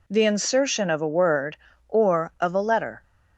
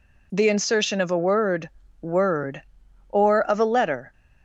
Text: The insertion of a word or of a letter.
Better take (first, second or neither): first